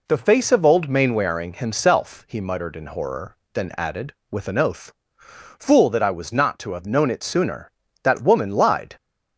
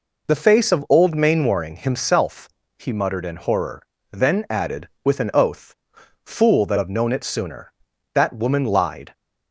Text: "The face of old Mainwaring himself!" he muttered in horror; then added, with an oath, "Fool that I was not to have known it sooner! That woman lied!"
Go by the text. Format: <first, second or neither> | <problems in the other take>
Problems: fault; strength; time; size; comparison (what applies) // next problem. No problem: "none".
first | skips "I was not to"; at 6.7 s